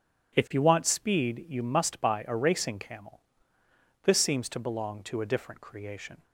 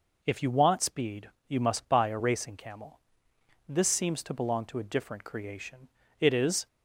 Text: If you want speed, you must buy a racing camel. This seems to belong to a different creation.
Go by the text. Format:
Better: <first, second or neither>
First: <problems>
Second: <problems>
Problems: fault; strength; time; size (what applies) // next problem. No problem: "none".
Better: first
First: none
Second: goes on to say "It is"; slight; from 6.1 s on; 0.48 s long